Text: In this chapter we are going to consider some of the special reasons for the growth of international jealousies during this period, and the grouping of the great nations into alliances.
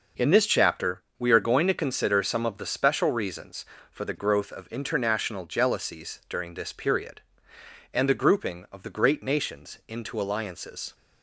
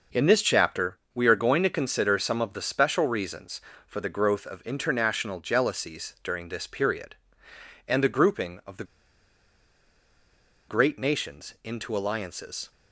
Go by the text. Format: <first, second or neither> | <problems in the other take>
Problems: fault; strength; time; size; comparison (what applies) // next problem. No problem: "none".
first | pauses between "chapter" and "we"; slight; at 0.9 s; 0.16 s long; slight in the first // pauses between "the" and "great"; strong; at 8.8 s; 1.8 s long